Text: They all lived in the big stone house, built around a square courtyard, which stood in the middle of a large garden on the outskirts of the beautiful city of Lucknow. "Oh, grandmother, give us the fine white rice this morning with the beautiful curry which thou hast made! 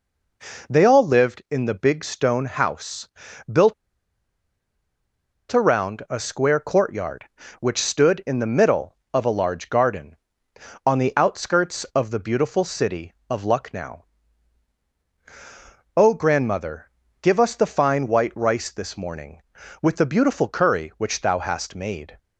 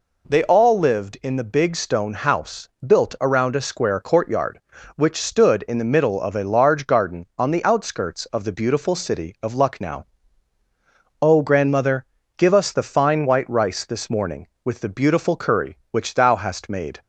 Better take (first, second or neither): second